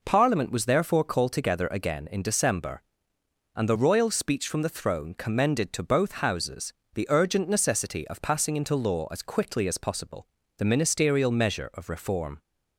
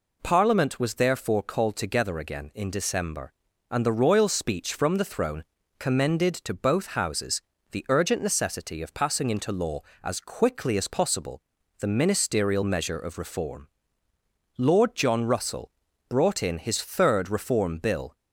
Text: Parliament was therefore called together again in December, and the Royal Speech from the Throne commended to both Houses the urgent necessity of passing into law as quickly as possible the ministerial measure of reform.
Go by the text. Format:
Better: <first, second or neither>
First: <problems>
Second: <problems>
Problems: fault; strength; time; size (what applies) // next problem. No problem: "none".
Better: first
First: pauses between "Houses" and "the"; slight; at 6.7 s; 0.22 s long // pauses between "possible" and "the"; slight; at 10.2 s; 0.30 s long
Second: pauses between "Throne" and "commended"; slight; at 5.4 s; 0.34 s long // pauses between "Houses" and "the"; slight; at 7.4 s; 0.30 s long // pauses between "possible" and "the"; at 11.3 s; 0.40 s long // goes on to say "Lord John Russell brought in his third Reform Bill"; strong; from 14.5 s on; 3.5 s long